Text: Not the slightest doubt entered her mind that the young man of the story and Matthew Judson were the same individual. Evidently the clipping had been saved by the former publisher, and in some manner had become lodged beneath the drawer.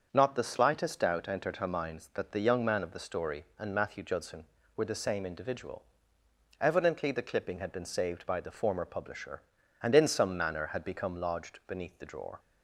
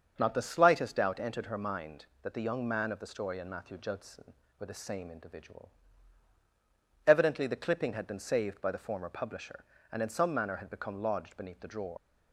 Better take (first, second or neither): first